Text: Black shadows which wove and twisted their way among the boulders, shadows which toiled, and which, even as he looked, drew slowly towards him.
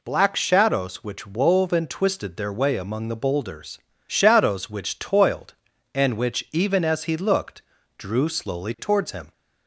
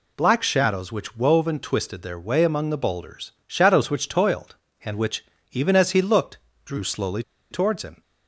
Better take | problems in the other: first | pauses between "slowly" and "towards"; slight; at 7.2 s; 0.28 s long

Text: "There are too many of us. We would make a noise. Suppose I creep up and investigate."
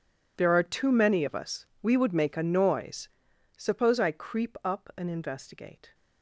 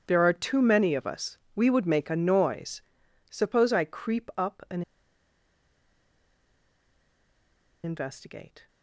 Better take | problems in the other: first | pauses between "and" and "investigate"; strong; at 4.8 s; 3.0 s long

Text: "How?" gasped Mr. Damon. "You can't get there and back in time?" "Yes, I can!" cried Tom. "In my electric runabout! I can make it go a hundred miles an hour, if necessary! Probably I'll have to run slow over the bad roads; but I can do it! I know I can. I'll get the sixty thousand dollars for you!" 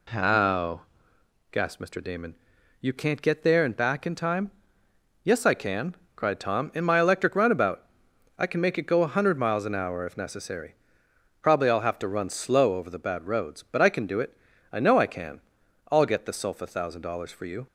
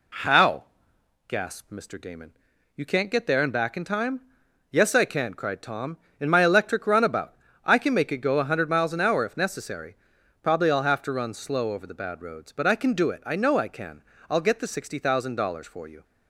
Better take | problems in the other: second | says "sulfa" for "sixty"; at 16.3 s

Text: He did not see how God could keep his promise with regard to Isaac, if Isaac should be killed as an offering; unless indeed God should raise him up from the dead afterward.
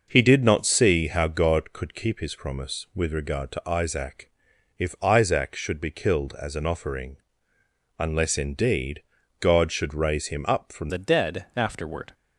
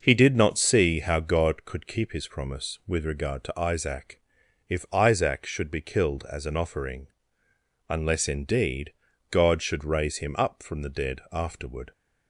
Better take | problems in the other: second | pauses between "indeed" and "God"; slight; at 9.0 s; 0.36 s long; slight in the second // changes voice at "the"; from 10.8 s on; 1.3 s long

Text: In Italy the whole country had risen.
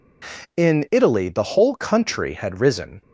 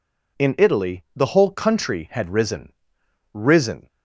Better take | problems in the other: first | says "risen" twice; at 3.3 s

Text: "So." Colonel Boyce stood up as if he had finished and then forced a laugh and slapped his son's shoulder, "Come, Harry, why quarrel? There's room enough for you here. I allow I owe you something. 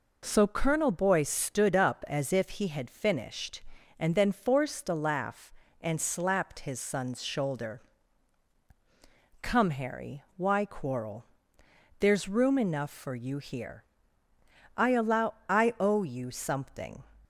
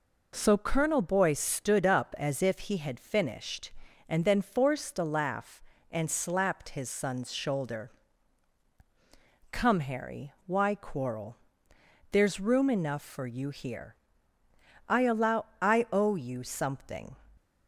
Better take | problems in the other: neither | pauses between "allow" and "I"; slight; the same in both

